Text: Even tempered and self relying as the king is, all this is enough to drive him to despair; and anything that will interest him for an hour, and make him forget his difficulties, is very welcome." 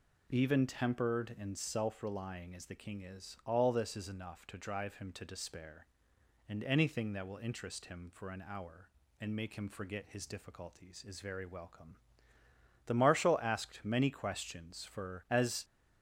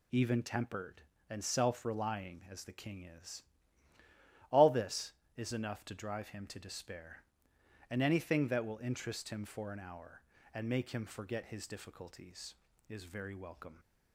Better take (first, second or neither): second